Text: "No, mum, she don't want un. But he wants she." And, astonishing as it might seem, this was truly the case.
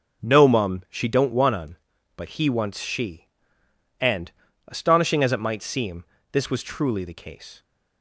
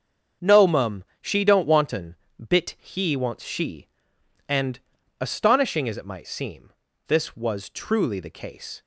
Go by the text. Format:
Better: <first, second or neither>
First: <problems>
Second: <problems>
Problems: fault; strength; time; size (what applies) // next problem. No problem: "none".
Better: first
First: none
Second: starts louder than the rest; strong; until 1.6 s; 7.5 dB // says "Bit" for "But"; at 2.4 s